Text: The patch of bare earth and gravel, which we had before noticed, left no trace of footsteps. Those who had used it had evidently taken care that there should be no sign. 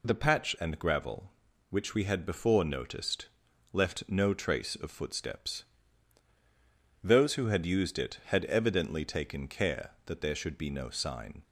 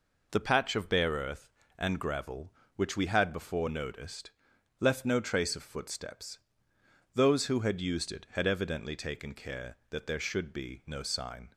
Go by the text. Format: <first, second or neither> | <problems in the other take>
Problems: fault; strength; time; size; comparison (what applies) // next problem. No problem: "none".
second | skips "of bare earth"; at 0.5 s